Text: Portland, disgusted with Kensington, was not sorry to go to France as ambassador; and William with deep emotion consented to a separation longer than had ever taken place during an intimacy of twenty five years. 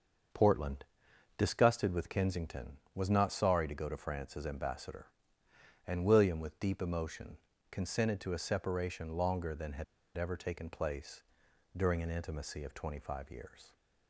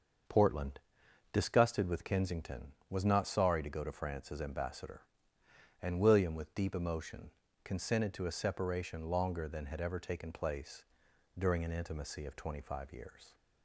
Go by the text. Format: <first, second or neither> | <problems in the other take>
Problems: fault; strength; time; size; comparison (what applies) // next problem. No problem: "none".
second | starts louder than the rest; until 1.8 s; 6.5 dB; also in the second // pauses between "emotion" and "consented"; slight; at 7.3 s; 0.34 s long; slight in the second // pauses between "had" and "ever"; slight; at 9.8 s; 0.32 s long // pauses between "place" and "during"; noticeable; at 11.2 s; 0.52 s long; noticeable in the second